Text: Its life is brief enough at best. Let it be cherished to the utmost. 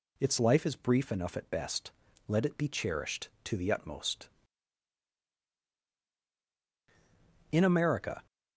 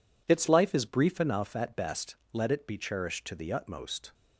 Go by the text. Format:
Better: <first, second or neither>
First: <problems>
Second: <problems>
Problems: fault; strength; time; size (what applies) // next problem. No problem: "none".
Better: second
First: goes on to say "In America"; noticeable; from 7.5 s on; 0.74 s long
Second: none